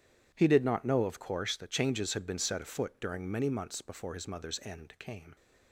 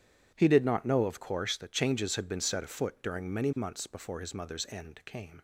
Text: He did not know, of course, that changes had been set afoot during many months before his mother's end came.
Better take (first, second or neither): neither